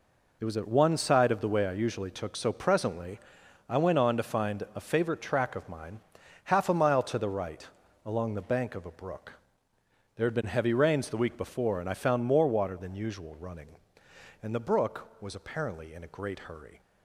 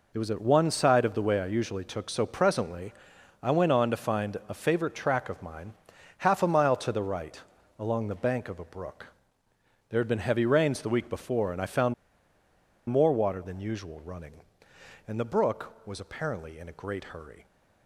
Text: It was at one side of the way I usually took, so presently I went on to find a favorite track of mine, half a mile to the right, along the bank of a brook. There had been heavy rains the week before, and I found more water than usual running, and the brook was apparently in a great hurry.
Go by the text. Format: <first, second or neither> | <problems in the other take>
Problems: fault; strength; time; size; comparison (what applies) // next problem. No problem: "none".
first | pauses between "presently" and "I"; noticeable; at 2.9 s; 0.50 s long; noticeable in the first // pauses between "found" and "more"; noticeable; at 11.9 s; 0.95 s long